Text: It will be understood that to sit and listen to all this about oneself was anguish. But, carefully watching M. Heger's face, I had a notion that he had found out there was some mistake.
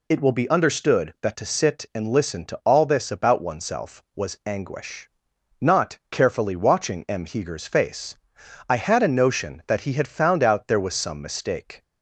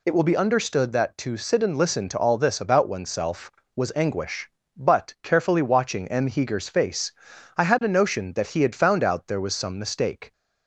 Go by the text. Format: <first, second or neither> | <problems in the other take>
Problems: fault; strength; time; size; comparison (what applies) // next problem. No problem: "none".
second | says "Not" for "But"; at 5.6 s